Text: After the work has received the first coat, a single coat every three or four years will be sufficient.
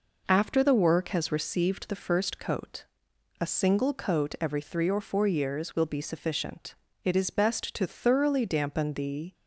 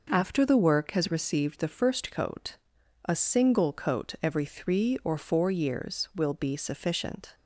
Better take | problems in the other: second | goes on to say "It is best to thoroughly dampen the"; strong; from 7.0 s on; 2.3 s long

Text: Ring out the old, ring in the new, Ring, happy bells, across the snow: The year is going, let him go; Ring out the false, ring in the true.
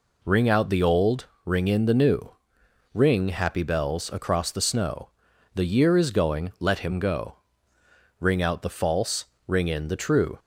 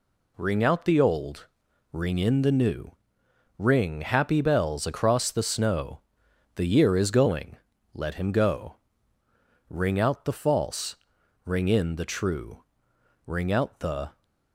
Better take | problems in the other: first | goes on to say "Ring out the"; noticeable; from 13.2 s on; 0.96 s long

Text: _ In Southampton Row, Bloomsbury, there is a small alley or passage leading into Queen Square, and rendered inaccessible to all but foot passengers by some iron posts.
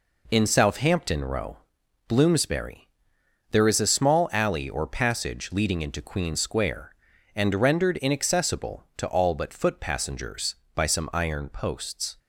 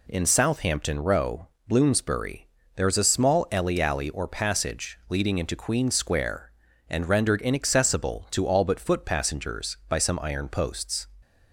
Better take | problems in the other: first | says "alley" twice; at 3.8 s

